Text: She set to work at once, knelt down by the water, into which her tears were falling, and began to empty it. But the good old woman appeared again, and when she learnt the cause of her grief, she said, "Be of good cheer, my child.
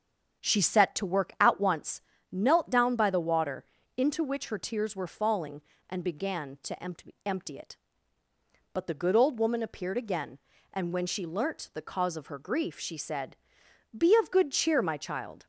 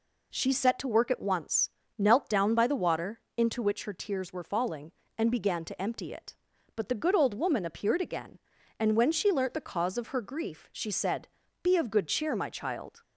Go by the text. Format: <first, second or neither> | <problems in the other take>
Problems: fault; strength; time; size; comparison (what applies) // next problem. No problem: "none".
second | starts louder than the rest; strong; until 1.4 s; 7.5 dB // says "empty" twice; at 7.2 s